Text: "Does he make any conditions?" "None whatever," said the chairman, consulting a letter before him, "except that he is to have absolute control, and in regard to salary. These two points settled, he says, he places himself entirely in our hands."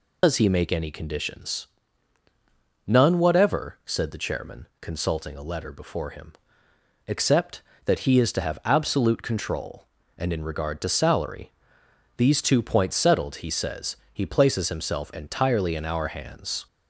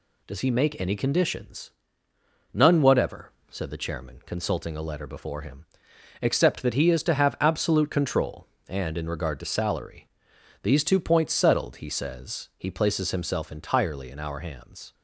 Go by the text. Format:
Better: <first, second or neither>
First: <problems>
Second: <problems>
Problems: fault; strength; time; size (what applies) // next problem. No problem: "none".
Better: second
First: loses the start of "Does"; at 0.2 s; 90 ms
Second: none